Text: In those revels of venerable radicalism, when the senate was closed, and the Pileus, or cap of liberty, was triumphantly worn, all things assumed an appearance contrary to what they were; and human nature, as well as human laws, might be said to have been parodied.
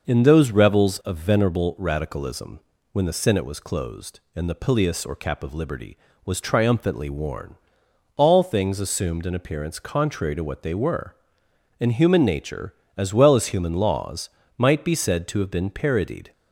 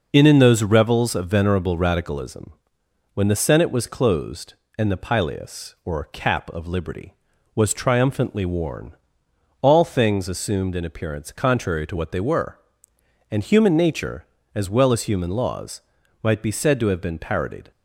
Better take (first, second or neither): first